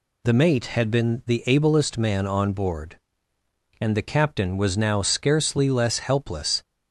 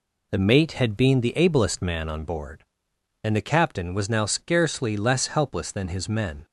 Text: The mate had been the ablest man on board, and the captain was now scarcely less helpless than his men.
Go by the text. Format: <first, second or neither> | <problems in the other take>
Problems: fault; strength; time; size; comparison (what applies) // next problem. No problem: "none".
second | stops before "than his men"; at 6.6 s